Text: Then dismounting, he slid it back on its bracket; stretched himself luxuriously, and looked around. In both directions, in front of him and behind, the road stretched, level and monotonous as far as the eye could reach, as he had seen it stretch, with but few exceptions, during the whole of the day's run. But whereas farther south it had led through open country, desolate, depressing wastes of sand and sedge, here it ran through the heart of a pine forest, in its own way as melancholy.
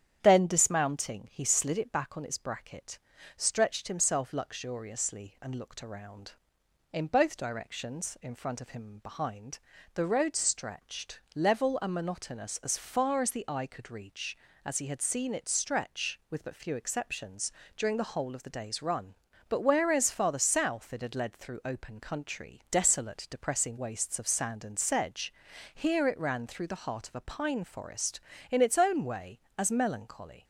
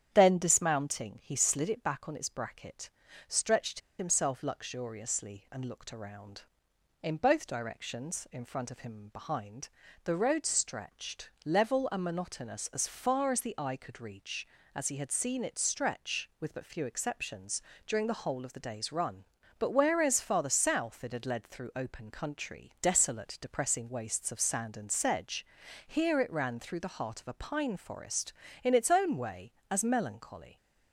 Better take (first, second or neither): first